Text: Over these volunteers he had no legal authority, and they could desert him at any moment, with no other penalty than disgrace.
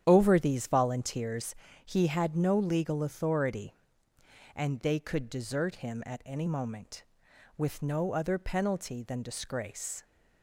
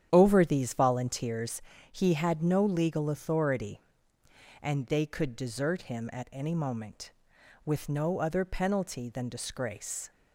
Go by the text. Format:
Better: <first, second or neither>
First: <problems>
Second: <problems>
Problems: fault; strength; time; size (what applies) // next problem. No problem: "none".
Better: neither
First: starts louder than the rest; strong; until 1.0 s; 9.5 dB // pauses between "volunteers" and "he"; slight; at 1.5 s; 0.32 s long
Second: starts louder than the rest; strong; until 1.1 s; 9.5 dB // pauses between "volunteers" and "he"; slight; at 1.5 s; 0.32 s long